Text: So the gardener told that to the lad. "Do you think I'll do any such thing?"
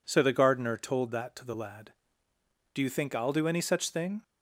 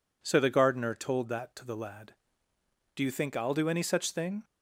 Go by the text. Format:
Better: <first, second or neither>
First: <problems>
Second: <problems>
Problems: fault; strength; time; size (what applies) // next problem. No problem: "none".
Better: neither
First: none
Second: none